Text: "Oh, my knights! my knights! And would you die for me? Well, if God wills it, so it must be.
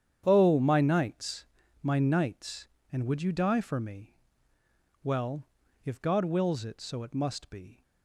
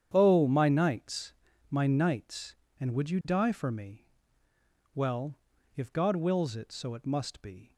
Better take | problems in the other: neither | starts louder than the rest; strong; the same in both

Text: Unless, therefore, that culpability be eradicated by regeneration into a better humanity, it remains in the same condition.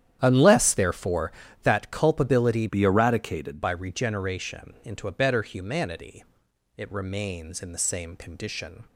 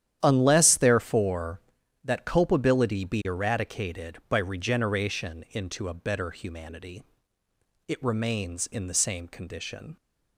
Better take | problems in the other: second | starts louder than the rest; strong; until 1.2 s; 10 dB; strong in the second // changes voice from "be" to "eradicated"; from 2.6 to 3.6 s; 1.0 s long

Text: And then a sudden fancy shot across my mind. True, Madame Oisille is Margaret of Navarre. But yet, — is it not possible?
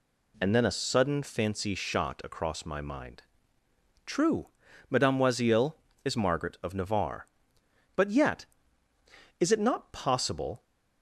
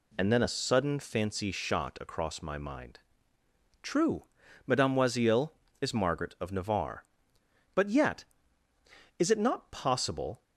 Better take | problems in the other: neither | none

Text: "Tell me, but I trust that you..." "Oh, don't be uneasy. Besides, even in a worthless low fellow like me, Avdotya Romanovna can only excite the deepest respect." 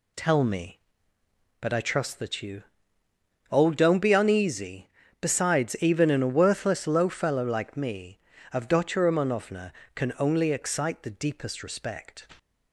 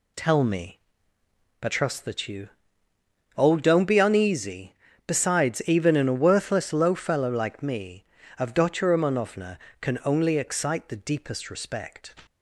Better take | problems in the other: first | skips "I"; at 1.6 s

